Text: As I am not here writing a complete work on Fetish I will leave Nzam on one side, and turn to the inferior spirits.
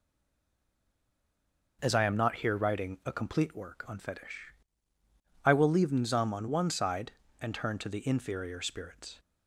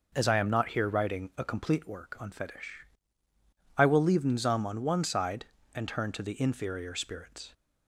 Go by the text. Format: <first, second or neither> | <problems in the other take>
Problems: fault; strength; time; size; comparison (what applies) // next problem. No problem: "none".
second | stays silent before the first word; noticeable; until 1.8 s; 1.8 s long // pauses between "Fetish" and "I"; noticeable; at 4.5 s; 0.92 s long; noticeable in the second